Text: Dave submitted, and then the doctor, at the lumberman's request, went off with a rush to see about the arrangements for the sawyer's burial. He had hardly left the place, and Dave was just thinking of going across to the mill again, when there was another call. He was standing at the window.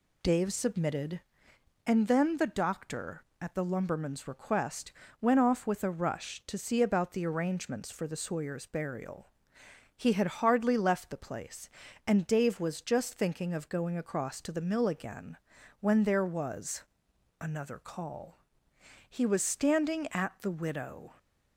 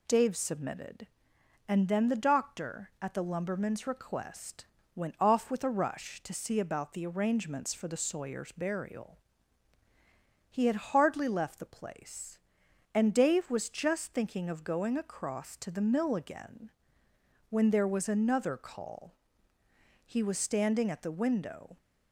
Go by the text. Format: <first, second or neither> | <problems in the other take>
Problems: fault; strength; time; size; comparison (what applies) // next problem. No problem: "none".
second | pauses between "was" and "another"; noticeable; at 16.8 s; 0.56 s long // says "widow" for "window"; at 20.5 s